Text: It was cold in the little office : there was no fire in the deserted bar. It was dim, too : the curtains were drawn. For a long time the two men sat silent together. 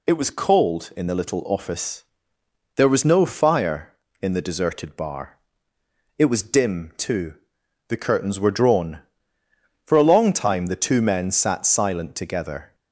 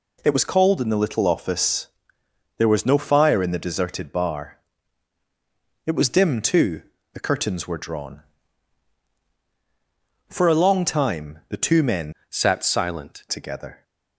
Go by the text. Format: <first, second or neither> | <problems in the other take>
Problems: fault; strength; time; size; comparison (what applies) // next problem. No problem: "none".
first | changes voice from "sat" to "silent"; from 12.2 to 13.2 s; 1.0 s long